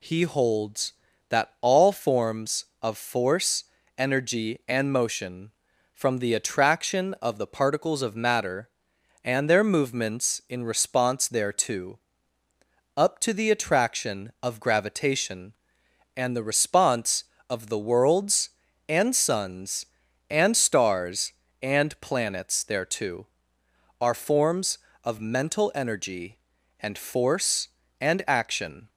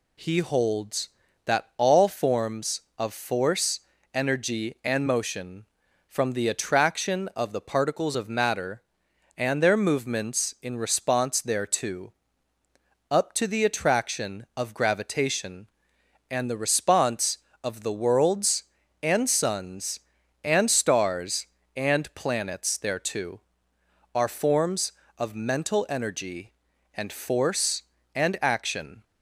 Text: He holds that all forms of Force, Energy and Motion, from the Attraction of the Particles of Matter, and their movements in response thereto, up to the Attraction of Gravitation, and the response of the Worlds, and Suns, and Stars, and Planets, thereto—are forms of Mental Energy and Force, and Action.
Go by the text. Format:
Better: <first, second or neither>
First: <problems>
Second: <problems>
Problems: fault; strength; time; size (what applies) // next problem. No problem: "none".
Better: neither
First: none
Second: none